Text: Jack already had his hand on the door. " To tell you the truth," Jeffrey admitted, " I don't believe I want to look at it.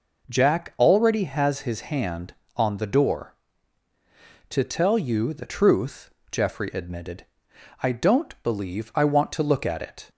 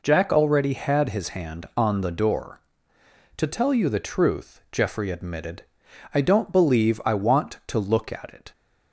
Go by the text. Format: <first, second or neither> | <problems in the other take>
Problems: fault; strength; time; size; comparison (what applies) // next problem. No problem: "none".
second | says "has" for "had"; at 1.2 s